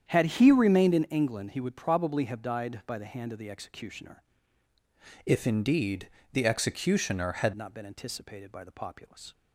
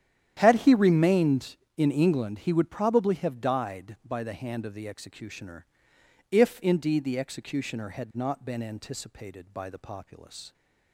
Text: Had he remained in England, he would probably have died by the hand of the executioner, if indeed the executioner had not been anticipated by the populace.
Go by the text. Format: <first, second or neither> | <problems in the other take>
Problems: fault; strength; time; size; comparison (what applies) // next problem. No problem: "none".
second | starts louder than the rest; strong; until 1.1 s; 8.5 dB; strong in the second // changes voice from "if" to "had"; from 5.2 to 7.5 s; 2.3 s long // pauses between "indeed" and "the"; slight; at 6.0 s; 0.24 s long